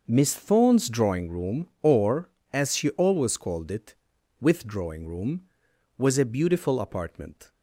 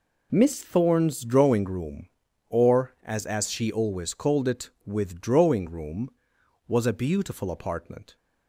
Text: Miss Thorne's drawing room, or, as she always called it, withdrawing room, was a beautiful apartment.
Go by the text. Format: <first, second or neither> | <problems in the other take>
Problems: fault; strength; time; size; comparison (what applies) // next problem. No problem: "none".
first | says "as" twice; at 3.2 s